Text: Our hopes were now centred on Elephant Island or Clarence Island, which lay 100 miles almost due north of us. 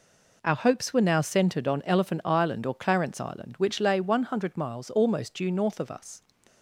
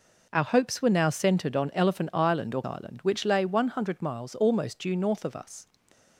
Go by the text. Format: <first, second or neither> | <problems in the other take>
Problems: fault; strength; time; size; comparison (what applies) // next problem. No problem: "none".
first | skips "Clarence"; at 2.6 s